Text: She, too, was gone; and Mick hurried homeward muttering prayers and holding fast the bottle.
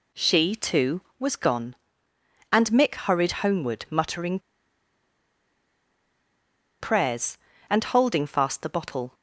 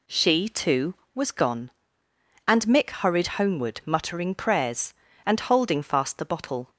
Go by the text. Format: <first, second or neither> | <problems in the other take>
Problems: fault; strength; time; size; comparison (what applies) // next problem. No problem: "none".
second | pauses between "muttering" and "prayers"; strong; at 4.3 s; 2.4 s long